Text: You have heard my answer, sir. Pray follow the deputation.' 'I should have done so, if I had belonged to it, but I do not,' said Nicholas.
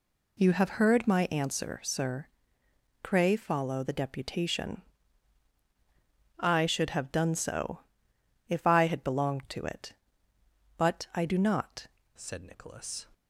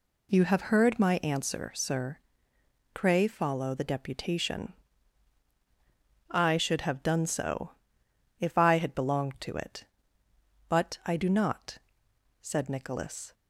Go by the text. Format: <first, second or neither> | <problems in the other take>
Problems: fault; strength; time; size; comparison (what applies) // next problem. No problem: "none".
second | changes voice at "said"; from 12.1 s on; 0.9 s long